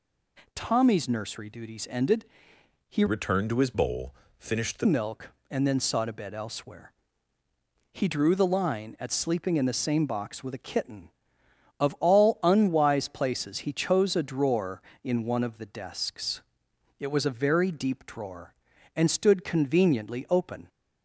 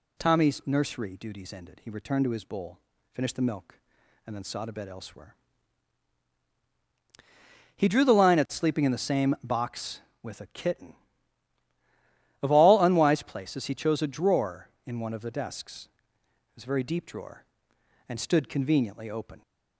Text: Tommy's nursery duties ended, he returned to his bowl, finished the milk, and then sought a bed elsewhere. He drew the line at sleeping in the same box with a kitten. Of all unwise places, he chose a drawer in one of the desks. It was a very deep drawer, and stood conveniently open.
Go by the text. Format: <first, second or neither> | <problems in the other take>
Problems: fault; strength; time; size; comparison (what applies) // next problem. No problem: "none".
second | changes voice from "returned" to "the"; from 3.0 to 4.8 s; 1.8 s long